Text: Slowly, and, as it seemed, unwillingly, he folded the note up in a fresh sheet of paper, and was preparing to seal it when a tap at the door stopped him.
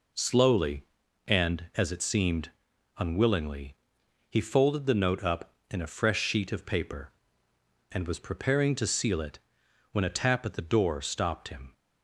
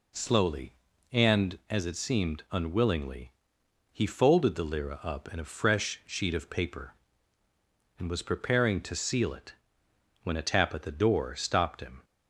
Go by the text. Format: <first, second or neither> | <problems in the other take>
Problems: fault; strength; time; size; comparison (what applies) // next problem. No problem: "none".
first | says "lira" for "note"; at 4.6 s // pauses between "it" and "when"; noticeable; at 9.5 s; 0.68 s long; noticeable in the first